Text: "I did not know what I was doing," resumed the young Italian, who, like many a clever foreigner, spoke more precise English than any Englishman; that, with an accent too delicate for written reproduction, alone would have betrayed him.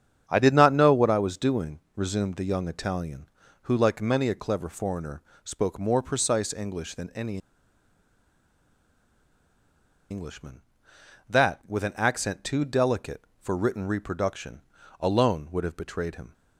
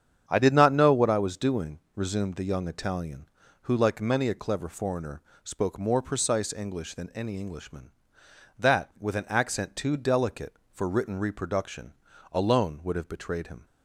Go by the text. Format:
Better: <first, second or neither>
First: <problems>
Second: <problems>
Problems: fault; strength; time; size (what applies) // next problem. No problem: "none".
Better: second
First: starts louder than the rest; strong; until 1.2 s; 8 dB // pauses between "any" and "Englishman"; strong; at 7.3 s; 2.7 s long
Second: starts louder than the rest; strong; until 1.2 s; 8 dB